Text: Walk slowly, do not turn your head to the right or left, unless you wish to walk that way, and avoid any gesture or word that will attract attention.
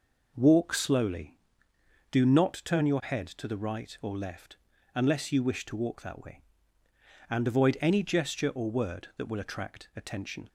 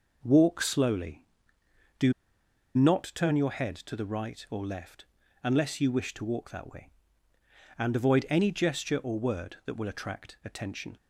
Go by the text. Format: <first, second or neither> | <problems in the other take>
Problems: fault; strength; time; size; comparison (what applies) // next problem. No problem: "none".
first | pauses between "do" and "not"; noticeable; at 2.1 s; 0.63 s long